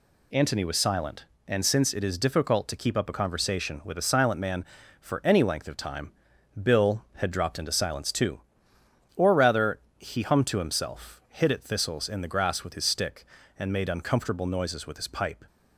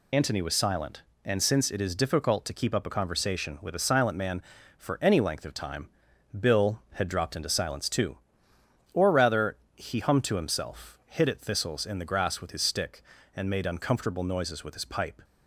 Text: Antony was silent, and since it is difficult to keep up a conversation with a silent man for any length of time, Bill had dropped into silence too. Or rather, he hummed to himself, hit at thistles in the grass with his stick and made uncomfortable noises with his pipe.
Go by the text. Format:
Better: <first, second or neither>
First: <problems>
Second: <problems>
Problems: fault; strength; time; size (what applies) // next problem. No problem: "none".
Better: first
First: none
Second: loses the start of "Antony"; at 0.1 s; 35 ms